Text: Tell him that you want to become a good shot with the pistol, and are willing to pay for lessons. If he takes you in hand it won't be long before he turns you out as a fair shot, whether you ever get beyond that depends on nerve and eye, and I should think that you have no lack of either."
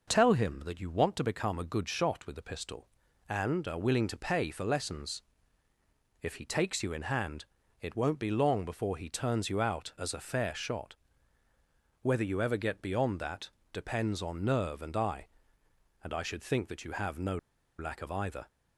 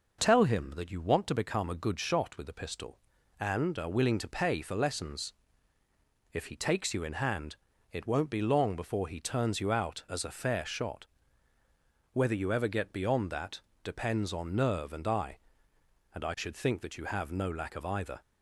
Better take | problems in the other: second | pauses between "hand" and "it"; slight; at 7.4 s; 0.36 s long; slight in the second // pauses between "that" and "depends"; slight; at 13.5 s; 0.20 s long; slight in the second // pauses between "no" and "lack"; at 17.3 s; 0.42 s long

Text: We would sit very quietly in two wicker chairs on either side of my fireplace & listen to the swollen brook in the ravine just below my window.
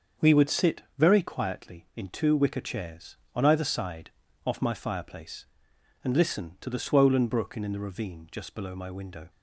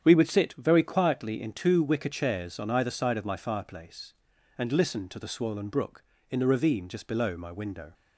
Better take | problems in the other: second | starts louder than the rest; until 1.3 s; 6.5 dB; strong in the second // pauses between "sit" and "very"; slight; at 0.8 s; 0.16 s long // says "off" for "of"; at 4.4 s

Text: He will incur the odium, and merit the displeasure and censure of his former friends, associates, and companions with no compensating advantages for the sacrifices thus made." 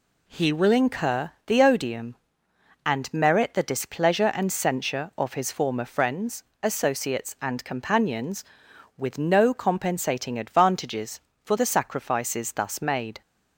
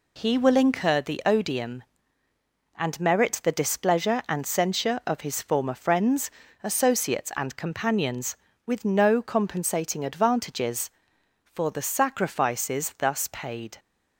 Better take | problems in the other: first | says "paid" for "made"; at 13.3 s

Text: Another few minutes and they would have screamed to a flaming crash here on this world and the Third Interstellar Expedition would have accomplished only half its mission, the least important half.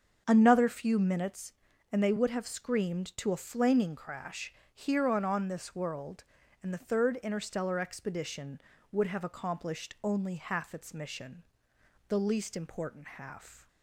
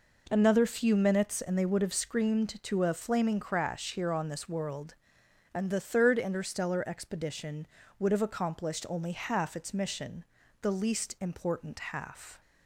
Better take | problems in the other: second | starts louder than the rest; strong; until 1.2 s; 7 dB // pauses between "crash" and "here"; slight; at 4.5 s; 0.20 s long // says "on" twice; at 5.2 s

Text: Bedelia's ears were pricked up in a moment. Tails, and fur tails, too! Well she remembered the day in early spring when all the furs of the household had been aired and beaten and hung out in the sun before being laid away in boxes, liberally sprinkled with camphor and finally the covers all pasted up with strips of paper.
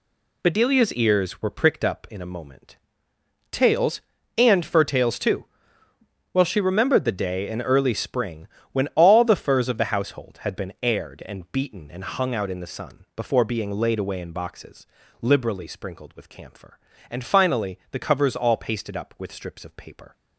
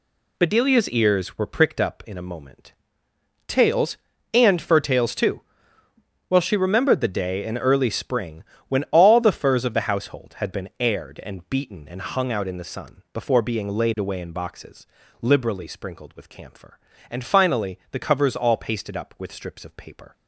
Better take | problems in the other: neither | pauses between "spring" and "when"; slight; the same in both

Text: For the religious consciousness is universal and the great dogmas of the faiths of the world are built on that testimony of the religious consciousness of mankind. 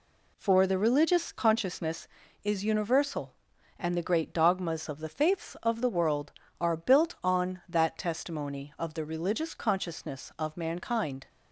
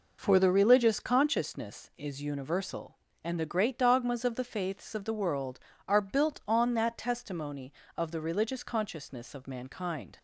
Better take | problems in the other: neither | none

